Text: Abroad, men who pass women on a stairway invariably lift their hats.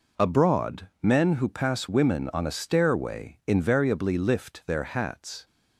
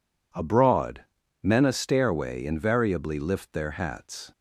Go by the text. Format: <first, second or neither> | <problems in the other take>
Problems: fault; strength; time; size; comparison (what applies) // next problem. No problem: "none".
first | skips "who pass women on"; at 1.6 s